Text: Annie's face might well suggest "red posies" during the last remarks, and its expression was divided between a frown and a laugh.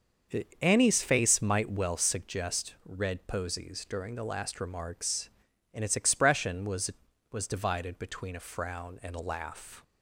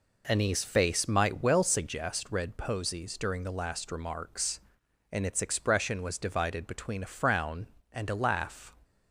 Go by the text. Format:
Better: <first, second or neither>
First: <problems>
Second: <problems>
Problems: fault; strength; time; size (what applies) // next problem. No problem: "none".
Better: second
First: starts louder than the rest; until 1.6 s; 6.5 dB // says "was" twice; at 7.3 s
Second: none